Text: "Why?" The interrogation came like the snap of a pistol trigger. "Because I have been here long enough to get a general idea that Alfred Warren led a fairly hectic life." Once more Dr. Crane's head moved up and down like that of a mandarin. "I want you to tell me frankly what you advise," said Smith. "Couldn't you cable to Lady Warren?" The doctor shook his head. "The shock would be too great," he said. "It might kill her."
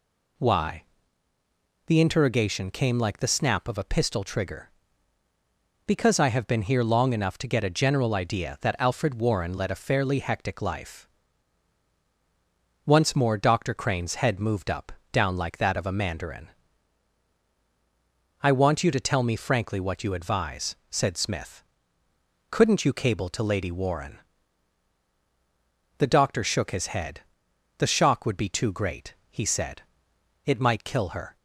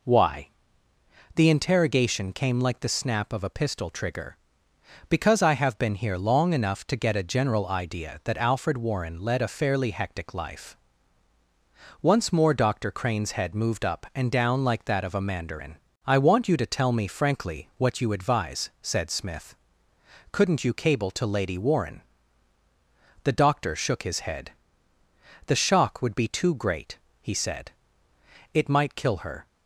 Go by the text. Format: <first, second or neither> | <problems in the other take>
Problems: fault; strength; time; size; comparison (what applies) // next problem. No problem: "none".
second | skips "and"; at 15.0 s